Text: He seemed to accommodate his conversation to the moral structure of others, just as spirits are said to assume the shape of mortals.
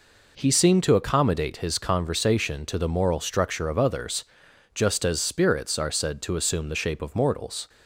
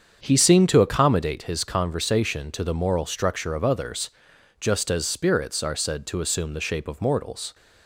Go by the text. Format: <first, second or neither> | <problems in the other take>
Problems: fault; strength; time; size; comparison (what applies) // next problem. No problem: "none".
first | starts louder than the rest; strong; until 1.3 s; 7.5 dB